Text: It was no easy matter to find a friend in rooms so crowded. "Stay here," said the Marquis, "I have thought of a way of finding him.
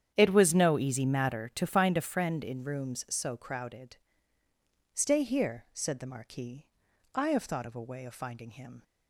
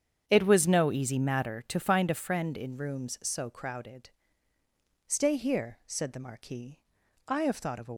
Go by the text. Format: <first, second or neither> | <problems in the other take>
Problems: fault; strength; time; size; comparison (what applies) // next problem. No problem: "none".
first | starts louder than the rest; strong; until 1.2 s; 8 dB; strong in the first // stops before "way of finding him"; at 7.9 s